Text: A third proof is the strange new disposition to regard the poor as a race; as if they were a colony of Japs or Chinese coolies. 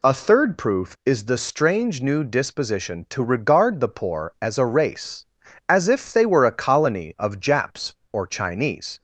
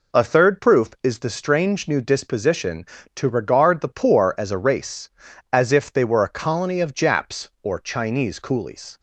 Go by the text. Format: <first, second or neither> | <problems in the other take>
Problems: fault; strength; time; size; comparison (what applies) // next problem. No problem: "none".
second | stops before "coolies"; at 8.9 s